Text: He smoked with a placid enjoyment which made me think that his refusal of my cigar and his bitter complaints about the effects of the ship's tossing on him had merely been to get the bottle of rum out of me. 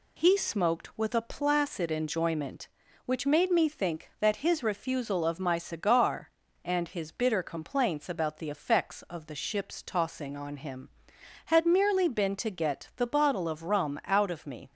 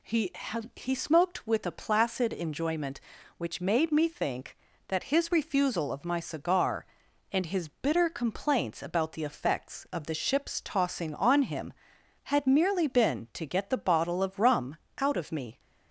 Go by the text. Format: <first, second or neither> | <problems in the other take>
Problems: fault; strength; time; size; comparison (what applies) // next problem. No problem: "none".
first | says "He" twice; at 0.7 s // pauses between "rum" and "out"; slight; at 14.7 s; 0.22 s long